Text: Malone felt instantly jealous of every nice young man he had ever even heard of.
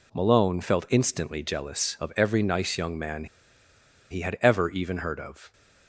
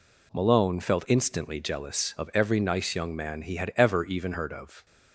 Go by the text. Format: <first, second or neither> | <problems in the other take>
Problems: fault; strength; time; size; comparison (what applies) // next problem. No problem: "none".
second | pauses between "man" and "he"; noticeable; at 3.2 s; 0.84 s long